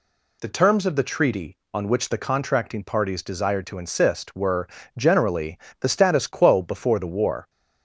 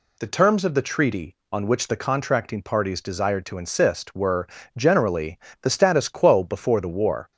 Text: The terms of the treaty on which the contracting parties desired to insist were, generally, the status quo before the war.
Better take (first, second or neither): neither